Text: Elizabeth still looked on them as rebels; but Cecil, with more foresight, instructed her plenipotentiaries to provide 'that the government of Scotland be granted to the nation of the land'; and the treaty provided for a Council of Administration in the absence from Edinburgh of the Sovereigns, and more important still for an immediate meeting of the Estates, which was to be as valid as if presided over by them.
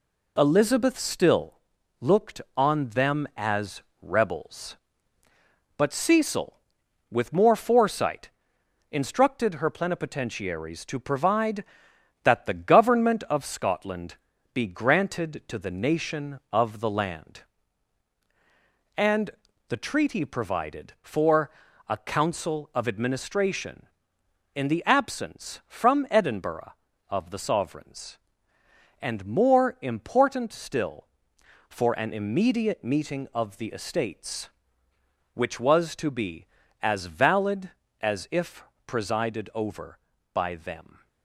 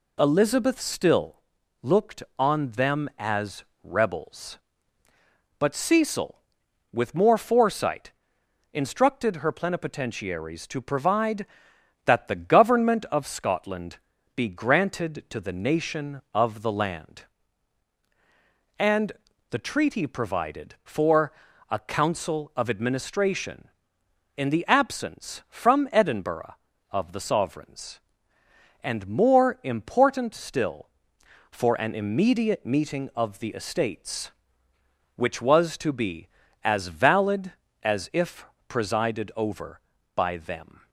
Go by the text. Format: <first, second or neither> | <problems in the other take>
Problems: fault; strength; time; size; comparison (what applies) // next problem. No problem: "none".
second | gets quieter; noticeable; throughout; 5 dB // pauses between "still" and "looked"; at 1.5 s; 0.44 s long; also in the second // pauses between "as" and "rebels"; slight; at 3.8 s; 0.22 s long; slight in the second // pauses between "Scotland" and "be"; slight; at 14.1 s; 0.36 s long; slight in the second // pauses between "and" and "the"; at 19.3 s; 0.38 s long; also in the second // pauses between "for" and "a"; at 21.4 s; 0.40 s long; also in the second // pauses between "if" and "presided"; slight; at 38.6 s; 0.24 s long; slight in the second